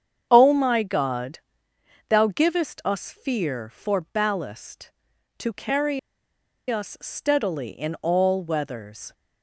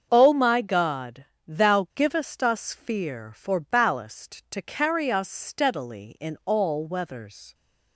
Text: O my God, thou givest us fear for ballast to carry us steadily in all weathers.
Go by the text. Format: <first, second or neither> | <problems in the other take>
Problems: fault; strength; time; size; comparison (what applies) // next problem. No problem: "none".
second | starts louder than the rest; strong; until 1.3 s; 8 dB; also in the second // pauses between "carry" and "us"; noticeable; at 5.9 s; 0.71 s long